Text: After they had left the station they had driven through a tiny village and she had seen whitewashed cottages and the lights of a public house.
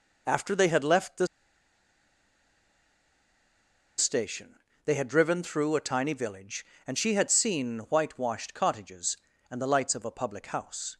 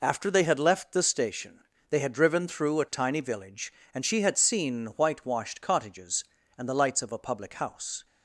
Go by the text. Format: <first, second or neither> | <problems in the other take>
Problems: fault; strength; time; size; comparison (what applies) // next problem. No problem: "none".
second | pauses between "the" and "station"; strong; at 1.2 s; 2.7 s long // pauses between "station" and "they"; slight; at 4.5 s; 0.28 s long; slight in the second